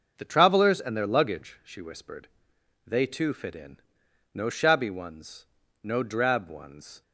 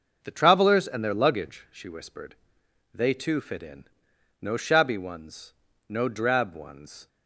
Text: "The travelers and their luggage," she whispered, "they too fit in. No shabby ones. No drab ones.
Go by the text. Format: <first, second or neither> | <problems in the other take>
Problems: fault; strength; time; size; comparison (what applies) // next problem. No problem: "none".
neither | none